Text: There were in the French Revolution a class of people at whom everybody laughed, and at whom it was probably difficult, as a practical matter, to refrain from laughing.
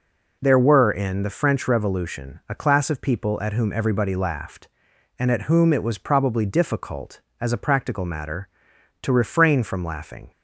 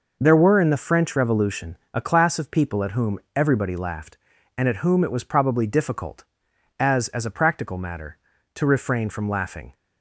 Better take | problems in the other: first | pauses between "Revolution" and "a"; slight; at 1.7 s; 0.16 s long // pauses between "whom" and "everybody"; slight; at 3.1 s; 0.16 s long // says "as" twice; at 7.0 s

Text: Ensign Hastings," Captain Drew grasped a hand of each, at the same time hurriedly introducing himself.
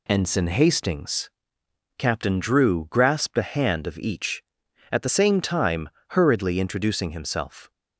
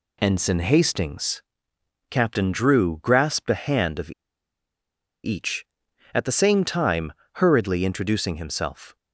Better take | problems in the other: first | pauses between "of" and "each"; at 4.1 s; 1.1 s long // pauses between "time" and "hurriedly"; slight; at 7.1 s; 0.22 s long; slight in the first

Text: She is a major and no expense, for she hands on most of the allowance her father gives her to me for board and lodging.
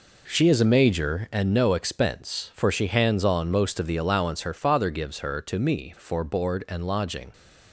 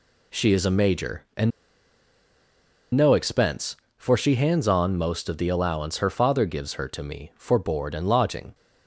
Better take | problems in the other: first | pauses between "and" and "no"; strong; at 1.5 s; 1.4 s long

